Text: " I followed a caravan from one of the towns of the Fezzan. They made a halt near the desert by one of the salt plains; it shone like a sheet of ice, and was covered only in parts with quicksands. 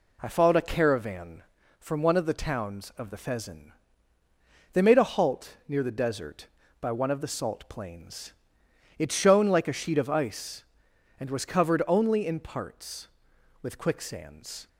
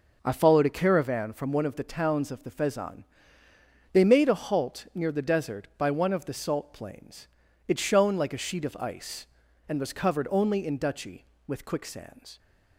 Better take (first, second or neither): first